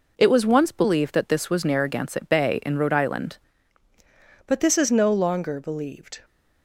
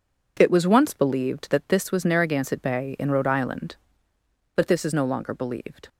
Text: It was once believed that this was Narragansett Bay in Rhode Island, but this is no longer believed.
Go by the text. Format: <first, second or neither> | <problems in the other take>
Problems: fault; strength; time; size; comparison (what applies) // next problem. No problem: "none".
second | changes voice at "but"; from 4.4 s on; 1.8 s long